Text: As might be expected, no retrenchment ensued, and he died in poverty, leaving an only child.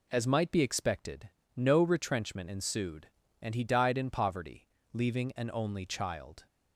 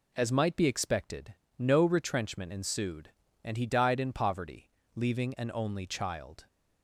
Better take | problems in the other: neither | none

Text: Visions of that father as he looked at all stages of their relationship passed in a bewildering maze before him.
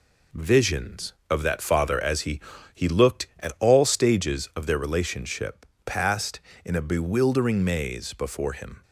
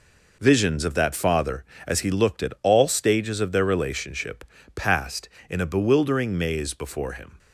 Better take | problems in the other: second | says "he" twice; at 2.7 s // pauses between "relationship" and "passed"; slight; at 5.6 s; 0.22 s long; slight in the second

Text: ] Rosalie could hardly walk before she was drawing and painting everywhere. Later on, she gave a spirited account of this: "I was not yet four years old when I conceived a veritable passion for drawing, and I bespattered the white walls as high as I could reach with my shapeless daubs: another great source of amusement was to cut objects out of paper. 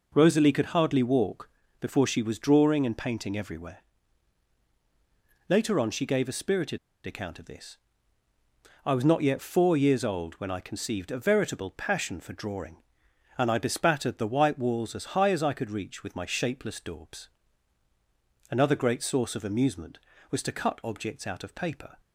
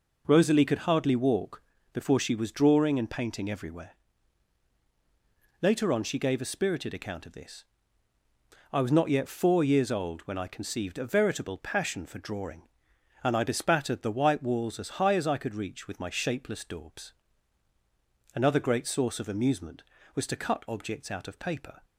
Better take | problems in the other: second | pauses between "walk" and "before"; slight; at 1.4 s; 0.30 s long; slight in the second // pauses between "spirited" and "account"; slight; at 6.7 s; 0.28 s long

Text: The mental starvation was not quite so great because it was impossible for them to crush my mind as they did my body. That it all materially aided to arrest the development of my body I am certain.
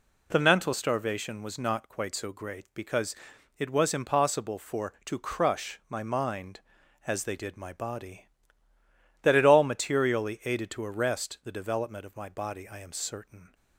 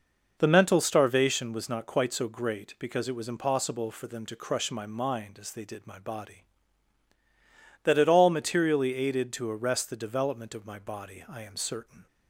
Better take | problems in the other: second | pauses between "because" and "it"; at 3.1 s; 0.42 s long // skips "them"; at 4.9 s

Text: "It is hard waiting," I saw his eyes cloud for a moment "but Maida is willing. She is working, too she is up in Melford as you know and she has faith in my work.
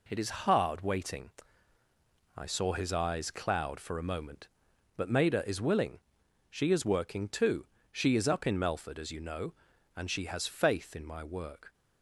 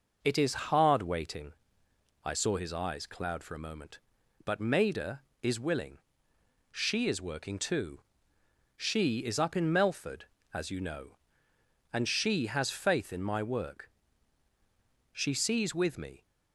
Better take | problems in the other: first | pauses between "too" and "she"; noticeable; at 8.0 s; 0.74 s long; slight in the first // goes on to say "She sees with me"; noticeable; from 15.1 s on; 1.1 s long

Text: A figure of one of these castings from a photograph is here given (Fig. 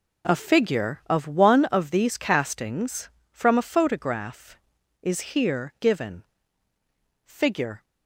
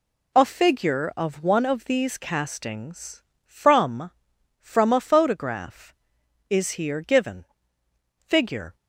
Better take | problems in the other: first | says "from" twice; at 4.6 s

